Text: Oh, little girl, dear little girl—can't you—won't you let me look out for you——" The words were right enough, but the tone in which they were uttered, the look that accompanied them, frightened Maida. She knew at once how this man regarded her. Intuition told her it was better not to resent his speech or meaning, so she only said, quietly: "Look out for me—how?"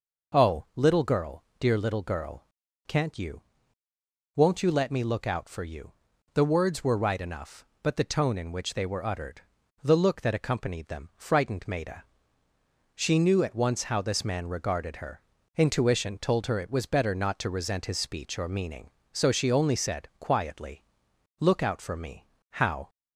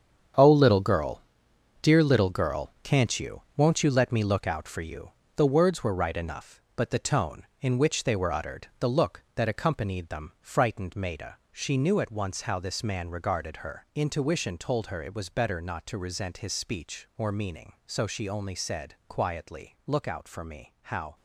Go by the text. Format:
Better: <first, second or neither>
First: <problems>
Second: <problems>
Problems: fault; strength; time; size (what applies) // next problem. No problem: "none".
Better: first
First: none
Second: gets quieter; strong; throughout; 10.5 dB